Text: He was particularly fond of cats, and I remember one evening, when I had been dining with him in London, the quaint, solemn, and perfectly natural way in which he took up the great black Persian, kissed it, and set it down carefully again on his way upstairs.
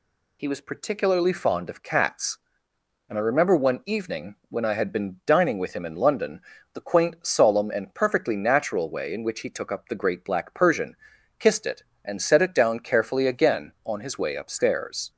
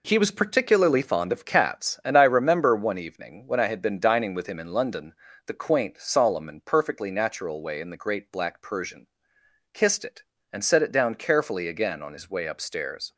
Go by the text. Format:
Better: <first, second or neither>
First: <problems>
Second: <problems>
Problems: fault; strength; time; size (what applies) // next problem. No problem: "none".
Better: first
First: none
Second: skips "which he took up"; at 7.8 s